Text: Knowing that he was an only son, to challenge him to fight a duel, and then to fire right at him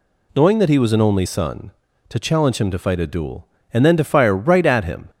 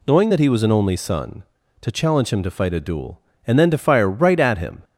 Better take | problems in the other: neither | none

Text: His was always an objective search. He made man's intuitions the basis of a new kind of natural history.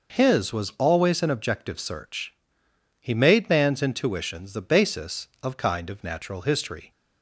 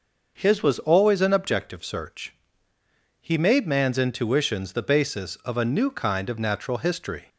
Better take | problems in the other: second | skips "a new"; at 5.5 s

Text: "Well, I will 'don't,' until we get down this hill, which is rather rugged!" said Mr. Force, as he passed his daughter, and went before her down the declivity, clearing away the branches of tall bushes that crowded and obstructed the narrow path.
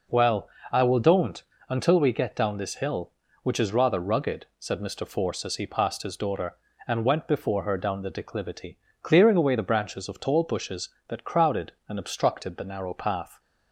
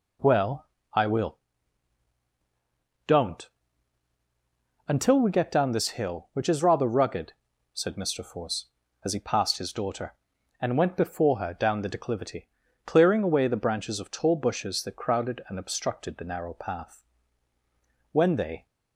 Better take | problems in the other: first | pauses between "will" and "don't"; strong; at 1.3 s; 1.6 s long // goes on to say "When they"; from 18.1 s on; 0.54 s long

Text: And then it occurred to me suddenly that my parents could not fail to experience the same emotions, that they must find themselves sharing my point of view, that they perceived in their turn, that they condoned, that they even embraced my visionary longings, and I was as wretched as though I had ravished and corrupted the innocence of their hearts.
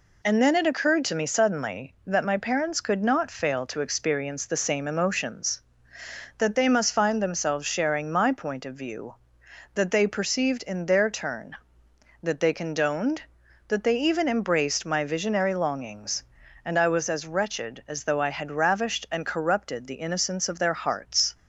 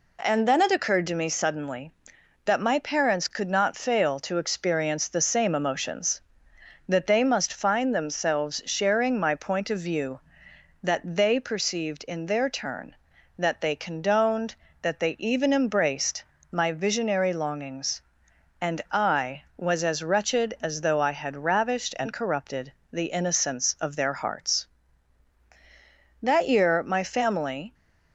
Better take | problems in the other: first | pauses between "embraced" and "my"; slight; at 16.2 s; 0.30 s long // pauses between "corrupted" and "the"; slight; at 22.7 s; 0.20 s long // goes on to say "That year my family"; from 26.2 s on; 1.5 s long

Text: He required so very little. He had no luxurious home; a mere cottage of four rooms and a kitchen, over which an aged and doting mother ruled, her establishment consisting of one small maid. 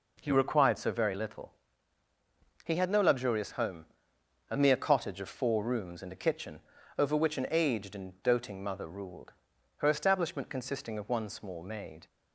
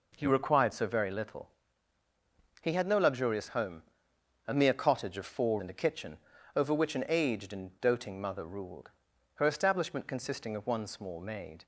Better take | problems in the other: first | skips "rooms"; at 5.5 s

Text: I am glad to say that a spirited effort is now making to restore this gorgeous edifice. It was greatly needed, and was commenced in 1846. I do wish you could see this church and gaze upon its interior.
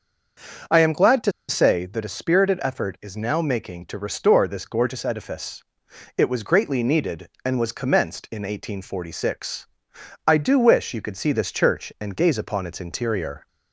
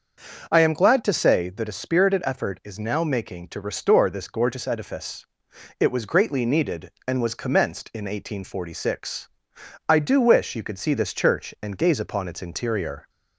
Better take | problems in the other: second | starts louder than the rest; until 1.8 s; 6.5 dB; also in the second // pauses between "to" and "say"; slight; at 1.3 s; 0.17 s long

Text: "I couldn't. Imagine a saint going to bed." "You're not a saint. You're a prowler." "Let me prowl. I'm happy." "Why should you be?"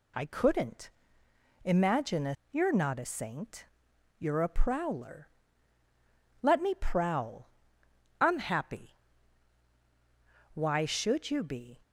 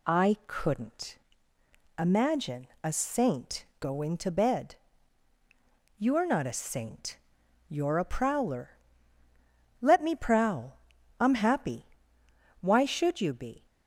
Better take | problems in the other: second | skips "saint going to bed"; at 2.4 s

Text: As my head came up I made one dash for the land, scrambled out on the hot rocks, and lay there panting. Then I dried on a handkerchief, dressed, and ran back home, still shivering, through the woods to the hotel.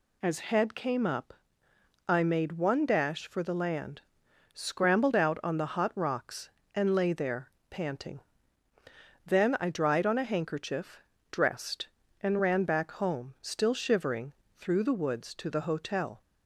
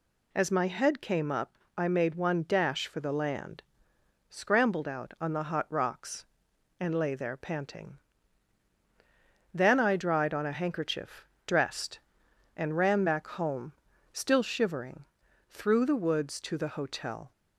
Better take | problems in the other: second | skips "my"; at 0.3 s // pauses between "up" and "I"; noticeable; at 1.3 s; 0.74 s long; slight in the second // pauses between "there" and "panting"; slight; at 7.4 s; 0.20 s long

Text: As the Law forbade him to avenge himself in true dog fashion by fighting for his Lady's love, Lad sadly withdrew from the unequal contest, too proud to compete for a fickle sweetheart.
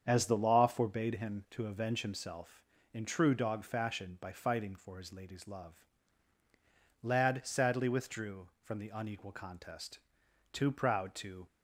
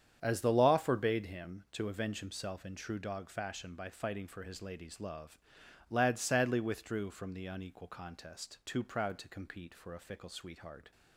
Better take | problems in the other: second | starts louder than the rest; strong; until 1.0 s; 7.5 dB; strong in the second // stops before "compete for a fickle sweetheart"; at 11.4 s

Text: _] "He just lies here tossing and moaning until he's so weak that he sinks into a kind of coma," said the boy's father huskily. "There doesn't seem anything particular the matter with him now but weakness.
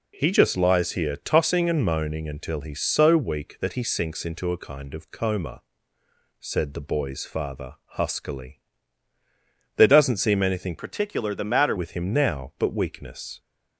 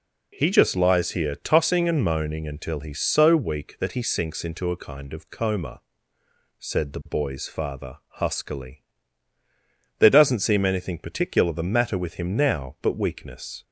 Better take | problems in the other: second | changes voice from "particular" to "matter"; from 10.7 to 11.7 s; 1.0 s long

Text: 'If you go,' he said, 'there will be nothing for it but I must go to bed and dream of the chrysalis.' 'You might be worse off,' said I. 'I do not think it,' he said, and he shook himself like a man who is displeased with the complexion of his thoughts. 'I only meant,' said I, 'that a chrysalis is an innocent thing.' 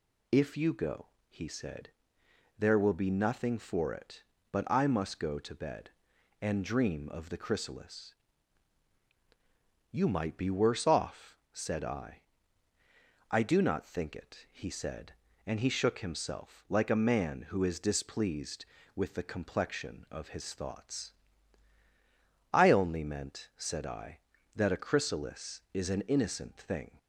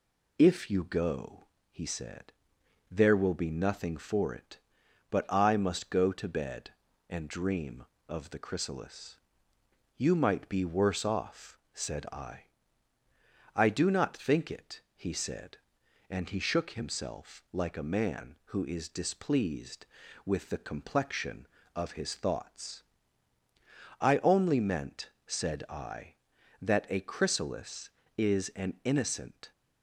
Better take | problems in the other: first | stops before "thing"; at 29.5 s

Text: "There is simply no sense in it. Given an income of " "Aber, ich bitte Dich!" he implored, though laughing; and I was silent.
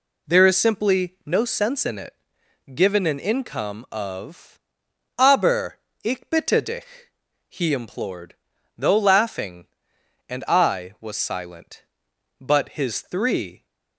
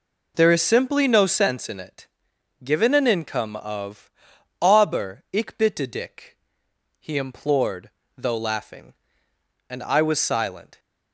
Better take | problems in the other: second | goes on to say "But his three"; noticeable; from 12.3 s on; 1.2 s long

